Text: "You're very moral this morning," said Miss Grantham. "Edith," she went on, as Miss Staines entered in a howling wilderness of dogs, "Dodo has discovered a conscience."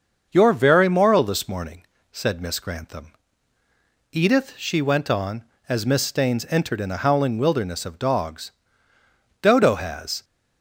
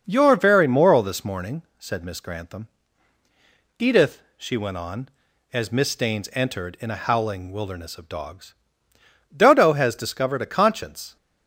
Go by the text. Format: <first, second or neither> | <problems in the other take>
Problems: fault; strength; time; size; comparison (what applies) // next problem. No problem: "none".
second | starts louder than the rest; until 1.3 s; 6.5 dB // stops before "discovered a conscience"; at 10.2 s